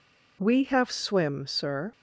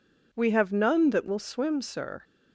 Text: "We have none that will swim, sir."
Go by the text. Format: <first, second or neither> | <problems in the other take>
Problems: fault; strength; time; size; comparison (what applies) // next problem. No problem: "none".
second | skips "none that will"; at 0.8 s